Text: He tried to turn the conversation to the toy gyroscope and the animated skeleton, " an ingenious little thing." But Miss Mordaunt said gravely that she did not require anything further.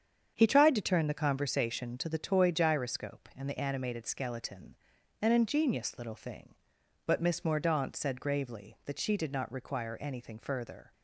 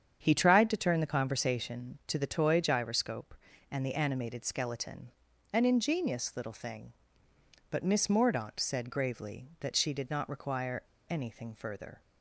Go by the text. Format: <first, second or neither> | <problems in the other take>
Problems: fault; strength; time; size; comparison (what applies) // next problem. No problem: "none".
first | starts louder than the rest; strong; until 1.2 s; 8 dB; strong in the first // pauses between "require" and "anything"; slight; at 10.8 s; 0.24 s long